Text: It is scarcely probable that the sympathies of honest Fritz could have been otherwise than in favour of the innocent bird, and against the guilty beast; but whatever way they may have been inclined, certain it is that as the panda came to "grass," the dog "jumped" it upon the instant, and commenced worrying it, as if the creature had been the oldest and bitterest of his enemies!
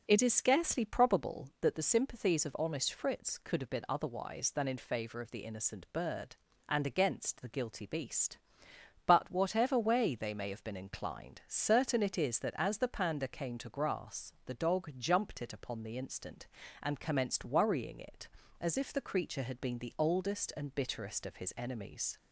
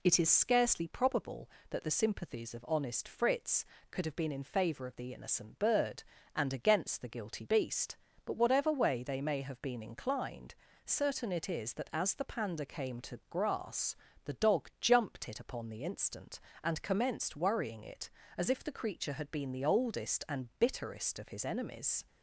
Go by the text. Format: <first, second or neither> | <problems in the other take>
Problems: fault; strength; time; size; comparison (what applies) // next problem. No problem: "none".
first | skips "otherwise than"; at 4.3 s